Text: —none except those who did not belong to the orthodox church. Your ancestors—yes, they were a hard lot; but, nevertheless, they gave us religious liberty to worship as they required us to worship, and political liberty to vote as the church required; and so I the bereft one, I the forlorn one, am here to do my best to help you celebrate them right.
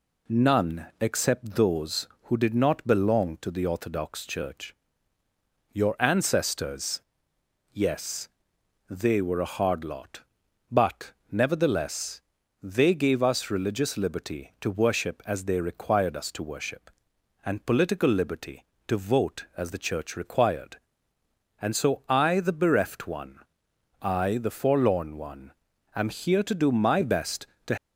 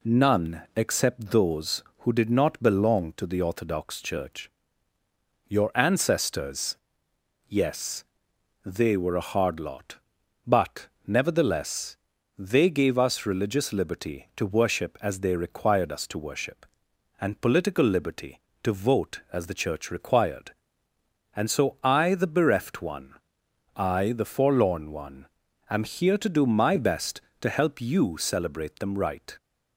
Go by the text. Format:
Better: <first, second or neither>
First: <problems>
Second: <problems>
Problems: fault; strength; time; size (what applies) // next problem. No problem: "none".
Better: second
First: stops before "help you celebrate them right"; at 27.7 s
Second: none